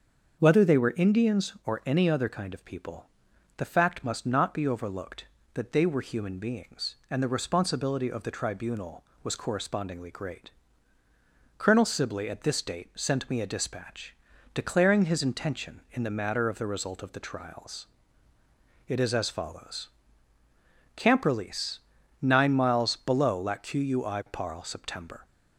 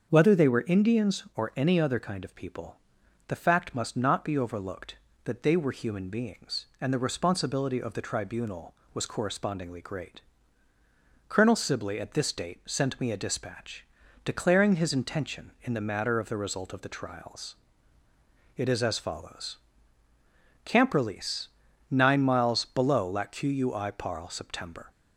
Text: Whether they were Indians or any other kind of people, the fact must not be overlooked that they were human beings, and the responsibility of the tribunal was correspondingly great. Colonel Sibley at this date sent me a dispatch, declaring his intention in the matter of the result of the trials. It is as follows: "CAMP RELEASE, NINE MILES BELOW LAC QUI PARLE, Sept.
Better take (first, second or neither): neither